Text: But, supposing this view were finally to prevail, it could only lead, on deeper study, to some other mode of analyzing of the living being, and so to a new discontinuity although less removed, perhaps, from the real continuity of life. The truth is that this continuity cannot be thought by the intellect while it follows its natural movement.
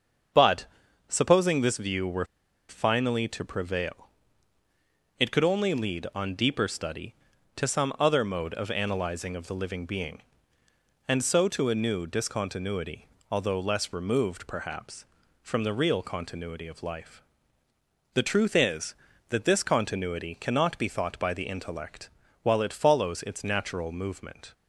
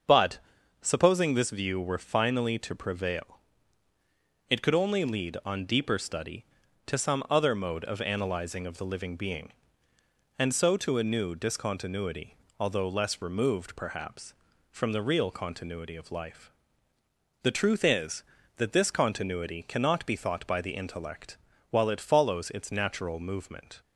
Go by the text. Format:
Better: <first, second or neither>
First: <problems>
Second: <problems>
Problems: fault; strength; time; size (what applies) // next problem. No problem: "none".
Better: second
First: starts louder than the rest; until 1.7 s; 6.5 dB // pauses between "were" and "finally"; at 2.2 s; 0.44 s long // pauses between "discontinuity" and "although"; slight; at 13.0 s; 0.26 s long // pauses between "intellect" and "while"; slight; at 22.0 s; 0.34 s long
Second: starts louder than the rest; until 1.5 s; 6.5 dB // pauses between "discontinuity" and "although"; slight; at 12.3 s; 0.26 s long // pauses between "intellect" and "while"; slight; at 21.3 s; 0.34 s long